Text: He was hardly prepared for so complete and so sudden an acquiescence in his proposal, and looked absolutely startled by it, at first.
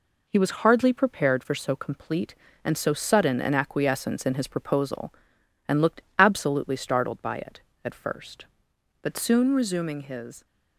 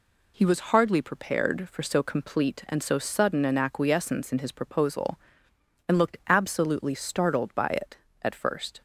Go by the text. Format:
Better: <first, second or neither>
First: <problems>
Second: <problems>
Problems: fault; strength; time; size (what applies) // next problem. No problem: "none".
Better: second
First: pauses between "looked" and "absolutely"; slight; at 6.0 s; 0.16 s long // goes on to say "But soon resuming his"; from 9.0 s on; 1.4 s long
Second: none